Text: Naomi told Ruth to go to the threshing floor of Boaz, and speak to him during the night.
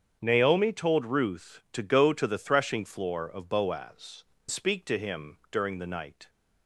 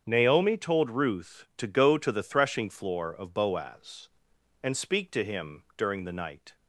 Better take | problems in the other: second | starts louder than the rest; strong; until 1.2 s; 8 dB; strong in the second // skips "and"; at 4.3 s

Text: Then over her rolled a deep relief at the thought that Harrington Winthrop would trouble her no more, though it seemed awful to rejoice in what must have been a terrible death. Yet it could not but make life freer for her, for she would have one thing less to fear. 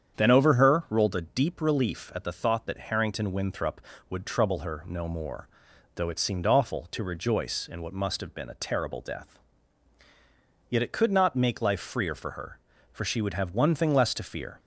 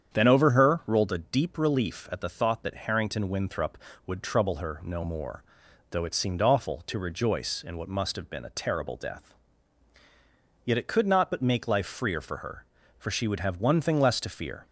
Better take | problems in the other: second | starts louder than the rest; strong; until 1.2 s; 8 dB; strong in the second // skips "but"; at 11.3 s

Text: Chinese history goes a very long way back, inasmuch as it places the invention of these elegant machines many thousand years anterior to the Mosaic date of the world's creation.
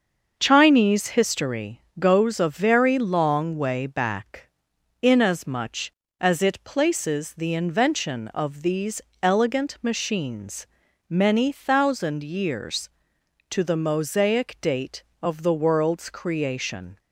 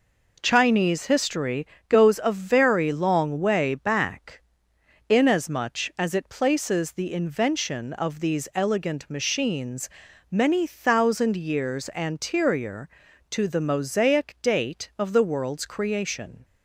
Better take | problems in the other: second | starts louder than the rest; until 1.4 s; 6.5 dB // pauses between "history" and "goes"; slight; at 1.8 s; 0.18 s long; slight in the second // pauses between "these" and "elegant"; slight; at 9.0 s; 0.22 s long // pauses between "machines" and "many"; at 10.6 s; 0.42 s long; also in the second // skips "anterior"; at 13.1 s

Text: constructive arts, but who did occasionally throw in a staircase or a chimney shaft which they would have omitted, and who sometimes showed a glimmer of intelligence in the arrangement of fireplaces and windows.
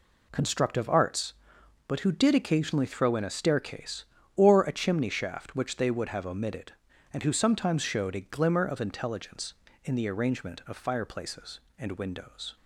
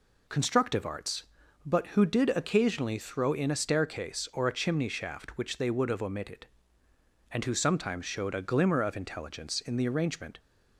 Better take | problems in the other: first | stops before "of fireplaces and windows"; at 10.3 s

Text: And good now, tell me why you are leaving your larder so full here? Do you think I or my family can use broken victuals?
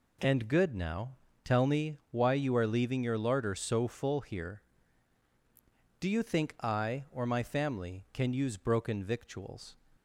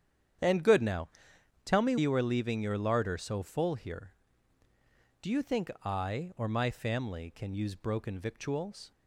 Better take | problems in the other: first | starts louder than the rest; strong; until 1.9 s; 9 dB // skips "why"; at 1.9 s

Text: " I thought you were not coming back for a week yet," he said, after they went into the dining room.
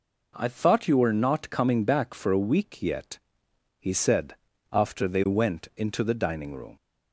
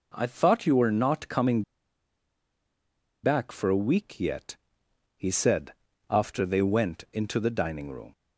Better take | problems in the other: first | pauses between "coming" and "back"; strong; at 1.6 s; 1.6 s long

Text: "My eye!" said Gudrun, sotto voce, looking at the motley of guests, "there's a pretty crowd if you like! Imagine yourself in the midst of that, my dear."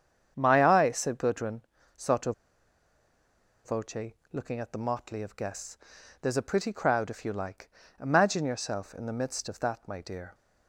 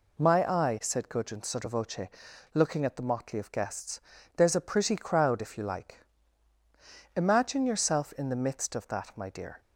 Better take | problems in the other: second | starts louder than the rest; strong; until 1.3 s; 8 dB // pauses between "sotto" and "voce"; strong; at 2.3 s; 1.3 s long

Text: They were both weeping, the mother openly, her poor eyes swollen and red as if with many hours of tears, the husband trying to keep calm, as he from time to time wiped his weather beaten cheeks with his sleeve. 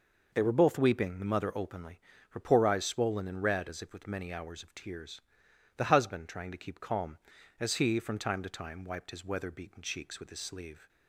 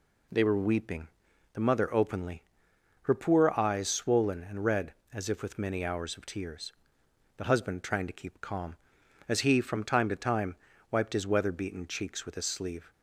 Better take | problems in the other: first | skips "both"; at 0.5 s // pauses between "time" and "wiped"; slight; at 10.5 s; 0.34 s long

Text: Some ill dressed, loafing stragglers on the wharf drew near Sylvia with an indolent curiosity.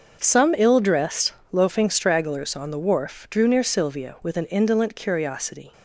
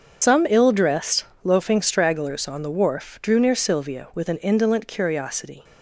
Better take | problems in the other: first | loses the start of "Some"; at 0.2 s; 90 ms // starts louder than the rest; until 1.4 s; 6.5 dB; also in the first

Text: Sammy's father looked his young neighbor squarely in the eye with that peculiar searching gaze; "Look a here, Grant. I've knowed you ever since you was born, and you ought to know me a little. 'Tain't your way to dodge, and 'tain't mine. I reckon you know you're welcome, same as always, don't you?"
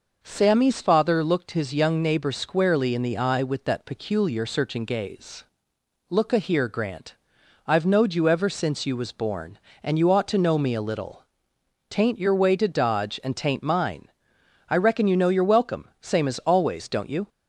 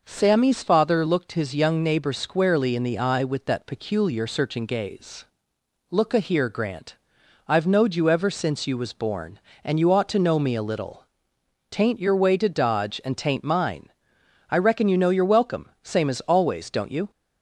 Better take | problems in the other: neither | none

